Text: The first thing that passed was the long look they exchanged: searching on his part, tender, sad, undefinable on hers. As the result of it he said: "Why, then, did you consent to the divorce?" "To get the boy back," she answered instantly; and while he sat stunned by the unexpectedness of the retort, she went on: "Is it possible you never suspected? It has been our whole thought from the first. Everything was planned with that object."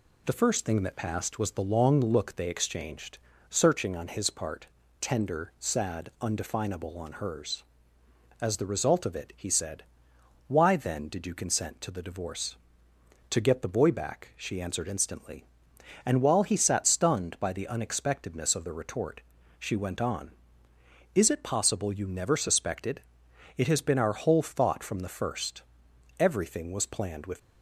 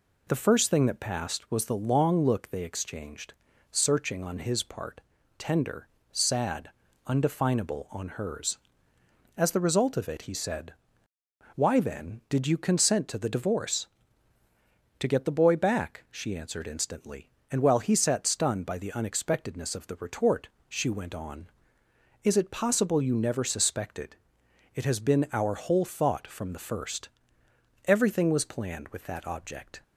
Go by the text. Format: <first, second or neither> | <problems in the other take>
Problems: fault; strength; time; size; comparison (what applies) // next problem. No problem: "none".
second | stops before "that object"; at 27.3 s